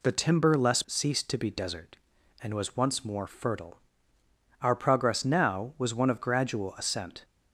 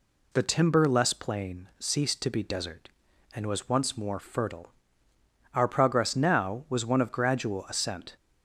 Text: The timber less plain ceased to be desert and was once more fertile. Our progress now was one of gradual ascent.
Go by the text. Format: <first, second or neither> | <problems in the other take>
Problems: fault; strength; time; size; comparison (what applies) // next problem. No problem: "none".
second | skips "plain"; at 0.8 s